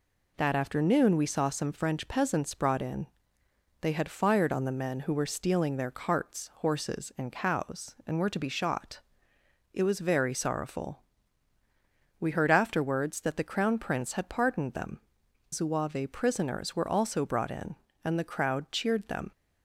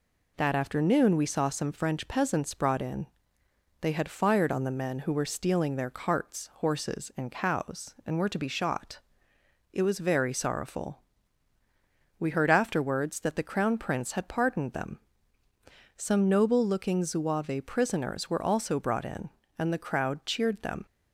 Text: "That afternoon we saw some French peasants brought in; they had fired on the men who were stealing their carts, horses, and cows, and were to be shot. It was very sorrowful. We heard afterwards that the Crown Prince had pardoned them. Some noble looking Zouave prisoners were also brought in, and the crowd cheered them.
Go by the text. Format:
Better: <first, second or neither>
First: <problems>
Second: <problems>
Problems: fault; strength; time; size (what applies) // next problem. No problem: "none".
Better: second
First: skips "Some noble looking"; at 15.2 s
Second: none